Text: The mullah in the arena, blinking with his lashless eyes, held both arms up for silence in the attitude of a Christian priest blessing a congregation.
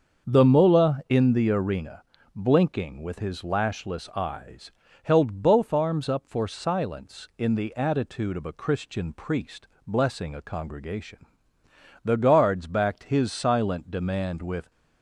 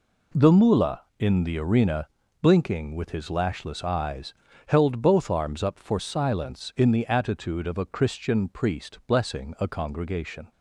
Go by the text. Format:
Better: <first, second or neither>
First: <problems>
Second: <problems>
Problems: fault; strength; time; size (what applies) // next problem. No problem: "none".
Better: second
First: starts louder than the rest; until 1.3 s; 6.5 dB // pauses between "priest" and "blessing"; slight; at 9.6 s; 0.18 s long // goes on to say "The guards backed his silent demand with"; strong; from 12.0 s on; 2.6 s long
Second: none